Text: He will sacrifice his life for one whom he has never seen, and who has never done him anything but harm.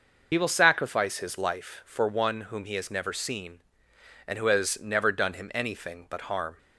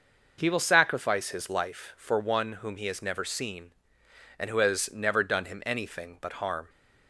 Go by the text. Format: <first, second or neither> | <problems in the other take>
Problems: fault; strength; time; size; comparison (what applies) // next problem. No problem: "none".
second | loses the start of "He"; at 0.3 s; 55 ms